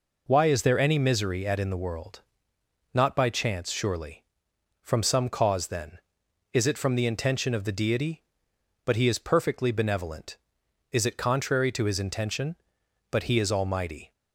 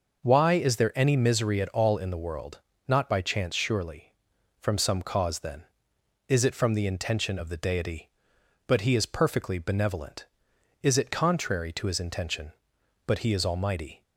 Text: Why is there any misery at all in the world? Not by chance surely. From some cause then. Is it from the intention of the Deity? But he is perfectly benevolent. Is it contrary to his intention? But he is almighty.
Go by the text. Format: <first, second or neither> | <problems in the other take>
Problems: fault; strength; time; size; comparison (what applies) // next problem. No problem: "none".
second | skips "all"; at 1.5 s